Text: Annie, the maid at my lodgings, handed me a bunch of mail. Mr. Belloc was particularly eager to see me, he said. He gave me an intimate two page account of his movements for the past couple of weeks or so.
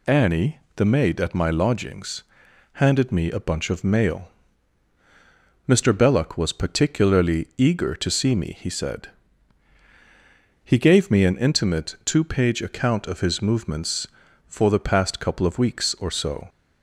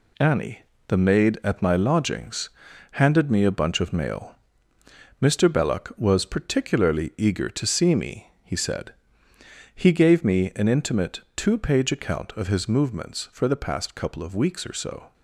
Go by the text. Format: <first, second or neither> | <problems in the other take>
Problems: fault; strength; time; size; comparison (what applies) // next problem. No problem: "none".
first | gets quieter; throughout; 7 dB